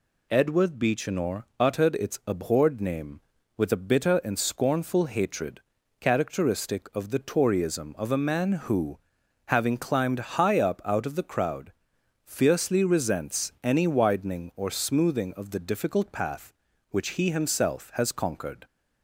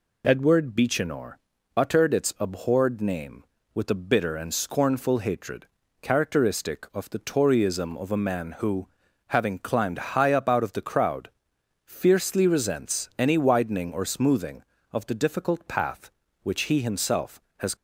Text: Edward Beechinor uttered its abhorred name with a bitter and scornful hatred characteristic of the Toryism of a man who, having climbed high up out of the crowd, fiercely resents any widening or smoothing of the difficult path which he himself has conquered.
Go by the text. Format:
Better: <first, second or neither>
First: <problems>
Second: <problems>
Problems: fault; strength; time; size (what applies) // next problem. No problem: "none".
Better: first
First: pauses between "Beechinor" and "uttered"; slight; at 1.4 s; 0.16 s long // pauses between "hatred" and "characteristic"; at 5.6 s; 0.40 s long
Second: pauses between "Beechinor" and "uttered"; at 1.3 s; 0.40 s long // pauses between "hatred" and "characteristic"; slight; at 5.6 s; 0.34 s long // stops before "conquered"; at 17.7 s